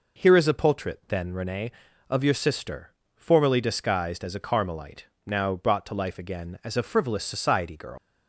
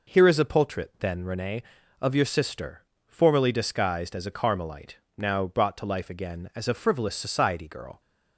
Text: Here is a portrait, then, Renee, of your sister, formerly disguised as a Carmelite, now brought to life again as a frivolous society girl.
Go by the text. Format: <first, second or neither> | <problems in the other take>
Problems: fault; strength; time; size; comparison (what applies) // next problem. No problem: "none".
second | leaves "girl" unfinished; at 7.9 s; 110 ms